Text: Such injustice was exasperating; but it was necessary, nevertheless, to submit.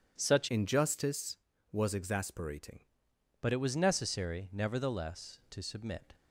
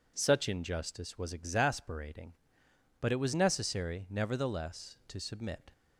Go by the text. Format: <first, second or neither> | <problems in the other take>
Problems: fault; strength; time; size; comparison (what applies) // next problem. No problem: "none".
second | changes voice from "injustice" to "exasperating"; from 0.5 to 2.8 s; 2.3 s long